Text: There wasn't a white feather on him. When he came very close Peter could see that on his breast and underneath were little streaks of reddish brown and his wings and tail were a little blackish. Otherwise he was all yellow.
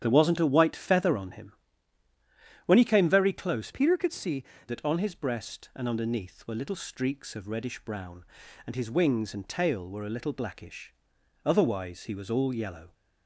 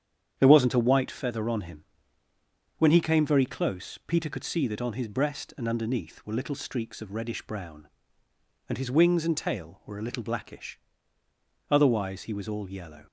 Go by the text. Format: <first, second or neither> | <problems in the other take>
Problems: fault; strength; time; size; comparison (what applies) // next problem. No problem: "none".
second | starts louder than the rest; strong; until 1.0 s; 9.5 dB; strong in the second // changes voice from "Peter" to "see"; from 3.7 to 4.4 s; 0.7 s long